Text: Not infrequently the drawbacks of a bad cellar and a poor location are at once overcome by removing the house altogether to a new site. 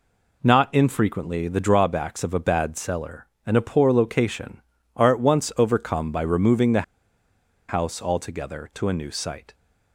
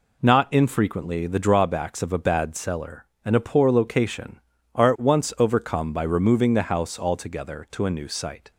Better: second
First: pauses between "the" and "house"; noticeable; at 6.8 s; 0.87 s long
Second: none

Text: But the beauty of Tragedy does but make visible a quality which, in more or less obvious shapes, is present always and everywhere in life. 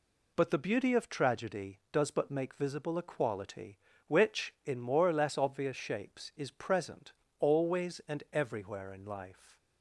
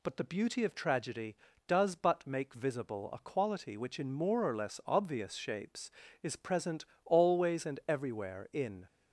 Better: first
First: pauses between "present" and "always"; slight; at 7.1 s; 0.26 s long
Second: pauses between "present" and "always"; slight; at 6.8 s; 0.22 s long // stops before "life"; at 8.8 s

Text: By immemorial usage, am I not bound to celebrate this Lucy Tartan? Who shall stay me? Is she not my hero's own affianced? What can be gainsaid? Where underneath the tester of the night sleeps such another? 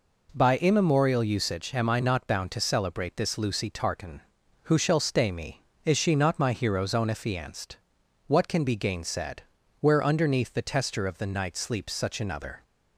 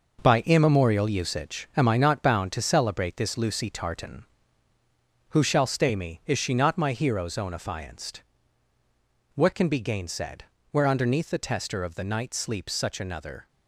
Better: first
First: none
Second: gets quieter; strong; throughout; 7.5 dB

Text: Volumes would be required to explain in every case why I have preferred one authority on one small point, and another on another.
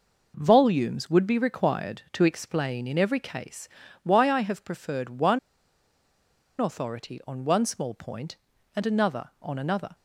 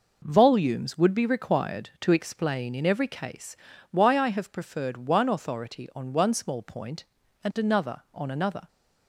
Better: second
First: pauses between "case" and "why"; slight; at 3.6 s; 0.34 s long // pauses between "one" and "authority"; at 5.3 s; 1.1 s long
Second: pauses between "case" and "why"; slight; at 3.5 s; 0.34 s long

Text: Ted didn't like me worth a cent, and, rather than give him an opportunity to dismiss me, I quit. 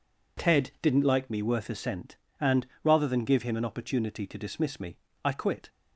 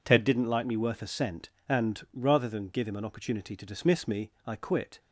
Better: neither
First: none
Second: none

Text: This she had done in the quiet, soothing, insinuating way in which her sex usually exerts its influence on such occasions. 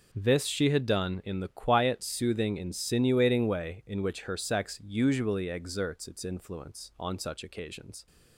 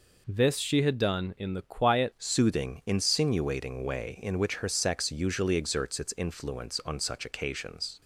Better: first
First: none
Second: changes voice at "soothing"; from 2.1 s on; 5.9 s long

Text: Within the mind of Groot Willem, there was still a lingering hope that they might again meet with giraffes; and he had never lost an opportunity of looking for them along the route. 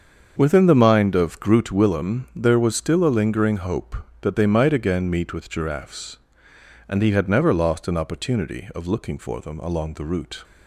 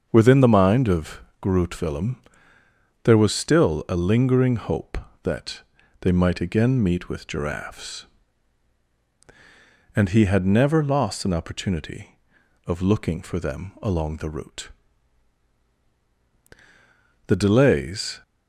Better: first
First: starts louder than the rest; until 1.3 s; 7 dB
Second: starts louder than the rest; until 1.1 s; 6.5 dB // pauses between "of" and "Groot"; slight; at 1.1 s; 0.22 s long // pauses between "that" and "they"; at 5.5 s; 0.40 s long // goes on to say "The delays"; noticeable; from 17.2 s on; 0.96 s long

